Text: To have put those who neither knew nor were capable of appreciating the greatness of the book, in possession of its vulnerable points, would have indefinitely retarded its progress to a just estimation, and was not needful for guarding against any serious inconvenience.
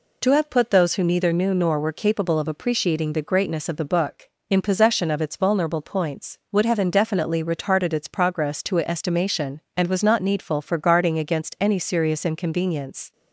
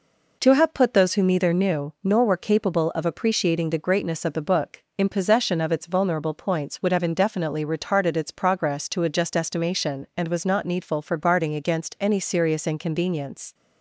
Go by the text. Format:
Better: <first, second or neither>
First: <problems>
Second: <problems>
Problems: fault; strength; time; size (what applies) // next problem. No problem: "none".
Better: second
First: skips "just"; at 8.8 s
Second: none